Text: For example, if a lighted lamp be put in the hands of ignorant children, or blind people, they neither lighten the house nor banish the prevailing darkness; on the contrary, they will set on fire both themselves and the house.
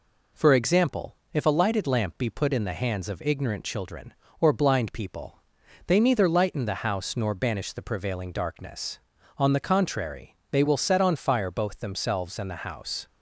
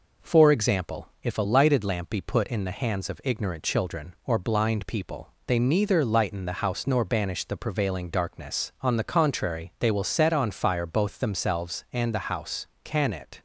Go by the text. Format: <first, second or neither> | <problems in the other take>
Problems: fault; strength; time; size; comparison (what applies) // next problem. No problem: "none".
first | goes on to say "Can it"; from 12.8 s on; 0.56 s long